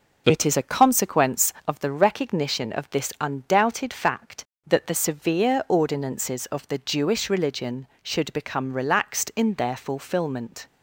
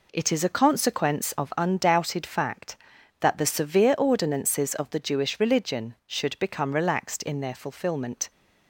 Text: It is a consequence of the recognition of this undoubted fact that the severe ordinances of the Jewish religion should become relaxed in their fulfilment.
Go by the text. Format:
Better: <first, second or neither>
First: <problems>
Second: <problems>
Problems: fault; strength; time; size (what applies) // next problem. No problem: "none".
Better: first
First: none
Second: skips "the recognition of this"; at 1.5 s